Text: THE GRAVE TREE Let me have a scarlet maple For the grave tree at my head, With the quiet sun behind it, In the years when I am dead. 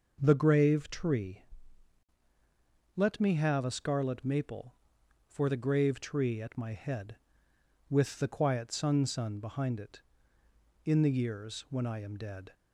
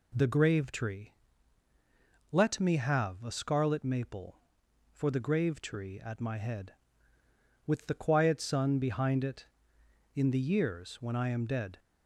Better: second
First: pauses between "TREE" and "Let"; strong; at 1.4 s; 1.5 s long // says "sun" twice; at 9.0 s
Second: pauses between "TREE" and "Let"; at 1.1 s; 1.2 s long

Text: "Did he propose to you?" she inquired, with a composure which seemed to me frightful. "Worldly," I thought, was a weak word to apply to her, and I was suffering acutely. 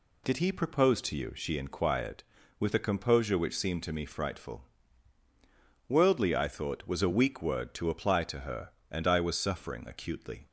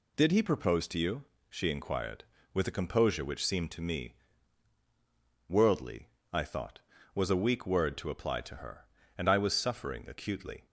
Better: first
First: none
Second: skips "frightful"; at 4.8 s

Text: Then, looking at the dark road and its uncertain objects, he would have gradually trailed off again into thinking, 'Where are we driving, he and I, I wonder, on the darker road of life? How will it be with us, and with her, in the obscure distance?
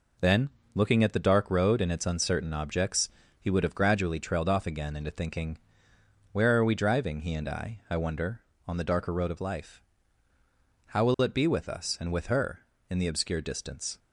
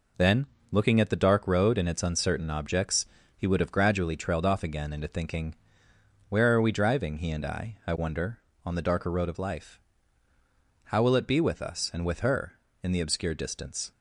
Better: neither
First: none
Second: none

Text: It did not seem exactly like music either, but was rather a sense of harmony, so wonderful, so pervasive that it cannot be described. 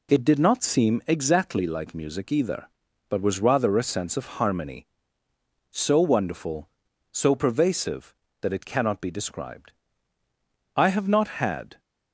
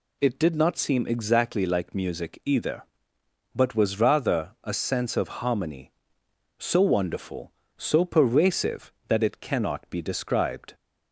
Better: second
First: goes on to say "I have not had"; noticeable; from 10.7 s on; 1.0 s long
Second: none

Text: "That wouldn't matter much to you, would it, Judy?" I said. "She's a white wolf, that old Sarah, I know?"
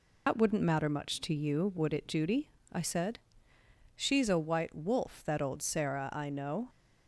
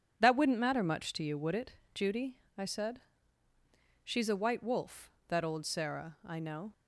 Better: second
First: loses the start of "That"; at 0.2 s; 95 ms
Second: none

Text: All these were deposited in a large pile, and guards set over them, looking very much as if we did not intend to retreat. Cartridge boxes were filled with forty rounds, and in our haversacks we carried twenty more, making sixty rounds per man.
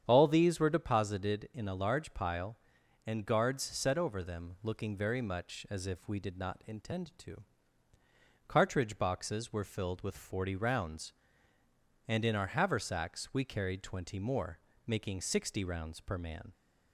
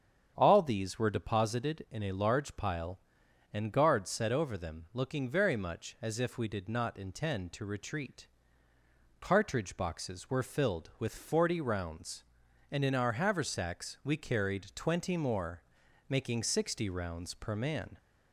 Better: second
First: starts louder than the rest; strong; until 1.0 s; 8.5 dB // skips "retreat"; at 7.9 s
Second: starts louder than the rest; strong; until 1.3 s; 8 dB

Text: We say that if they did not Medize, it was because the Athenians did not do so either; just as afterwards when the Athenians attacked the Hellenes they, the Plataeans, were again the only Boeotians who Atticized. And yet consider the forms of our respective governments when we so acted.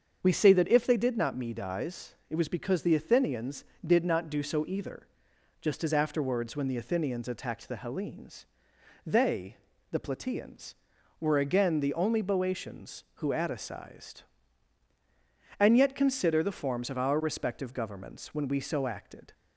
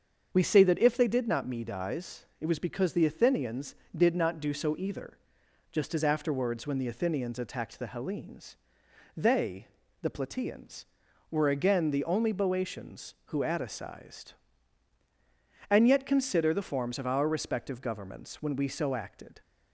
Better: neither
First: starts louder than the rest; until 1.2 s; 7 dB // pauses between "Hellenes" and "they"; noticeable; at 8.4 s; 0.58 s long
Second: starts louder than the rest; until 1.3 s; 7 dB // pauses between "Hellenes" and "they"; noticeable; at 8.5 s; 0.58 s long

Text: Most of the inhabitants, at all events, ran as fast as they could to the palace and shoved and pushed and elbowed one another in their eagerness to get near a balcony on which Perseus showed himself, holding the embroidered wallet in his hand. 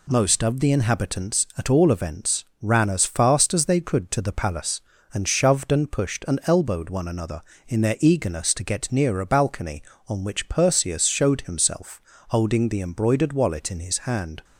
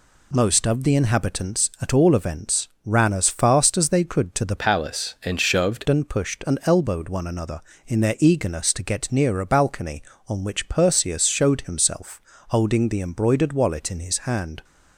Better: first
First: none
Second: changes voice from "palace" to "shoved"; from 4.5 to 5.8 s; 1.3 s long

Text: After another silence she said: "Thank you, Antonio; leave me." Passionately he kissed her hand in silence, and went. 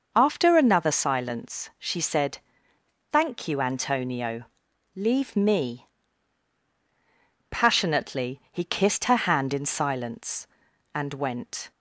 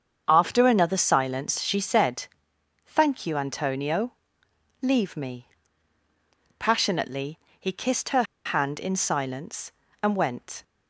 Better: first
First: none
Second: starts louder than the rest; until 1.2 s; 7 dB // pauses between "Passionately" and "he"; slight; at 7.3 s; 0.22 s long // pauses between "her" and "hand"; slight; at 8.2 s; 0.22 s long

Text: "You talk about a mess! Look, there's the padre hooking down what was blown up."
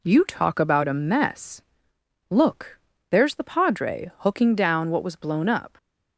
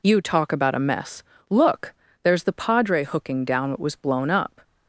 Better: neither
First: none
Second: none

